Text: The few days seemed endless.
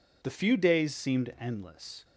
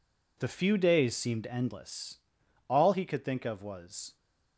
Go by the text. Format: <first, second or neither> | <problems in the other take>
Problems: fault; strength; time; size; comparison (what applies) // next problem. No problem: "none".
first | goes on to say "All he could think of was"; from 2.6 s on; 1.4 s long